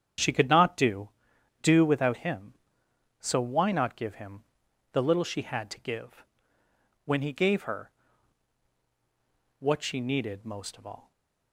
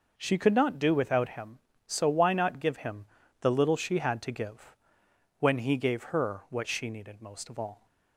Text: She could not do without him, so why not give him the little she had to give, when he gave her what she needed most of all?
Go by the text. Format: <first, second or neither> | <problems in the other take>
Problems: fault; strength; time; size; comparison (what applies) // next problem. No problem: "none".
second | starts louder than the rest; strong; until 1.6 s; 8.5 dB // says "do" twice; at 1.6 s // pauses between "him" and "the"; noticeable; at 4.4 s; 0.48 s long; slight in the second // pauses between "her" and "what"; strong; at 7.9 s; 1.6 s long // stays silent after the last word; slight; from 11.0 s on; 0.5 s long